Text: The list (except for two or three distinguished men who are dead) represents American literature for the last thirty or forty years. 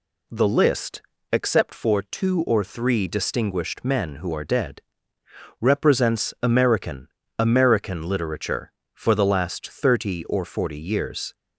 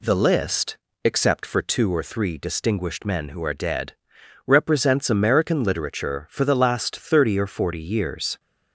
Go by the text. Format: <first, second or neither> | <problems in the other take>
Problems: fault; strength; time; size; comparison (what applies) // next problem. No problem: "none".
second | says "American" twice; at 7.3 s